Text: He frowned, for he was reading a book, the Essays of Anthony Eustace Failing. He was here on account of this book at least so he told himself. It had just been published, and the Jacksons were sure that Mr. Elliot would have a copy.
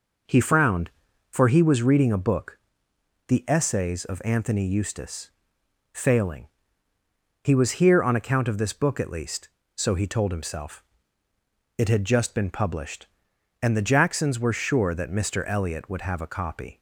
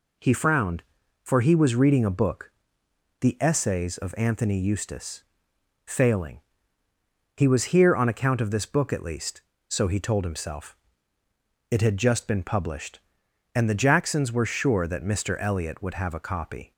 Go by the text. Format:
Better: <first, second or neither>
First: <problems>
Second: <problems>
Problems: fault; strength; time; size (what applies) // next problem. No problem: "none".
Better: second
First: starts louder than the rest; noticeable; until 1.7 s; 5 dB // pauses between "Eustace" and "Failing"; noticeable; at 5.2 s; 0.64 s long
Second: pauses between "Eustace" and "Failing"; noticeable; at 5.2 s; 0.64 s long